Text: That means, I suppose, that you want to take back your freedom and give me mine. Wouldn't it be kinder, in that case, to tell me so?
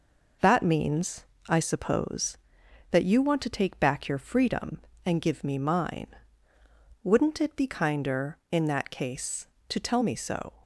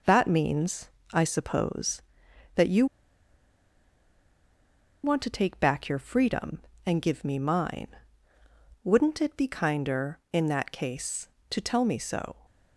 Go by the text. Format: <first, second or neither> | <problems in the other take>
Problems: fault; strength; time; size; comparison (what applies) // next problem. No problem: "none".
first | pauses between "you" and "want"; strong; at 2.8 s; 2.1 s long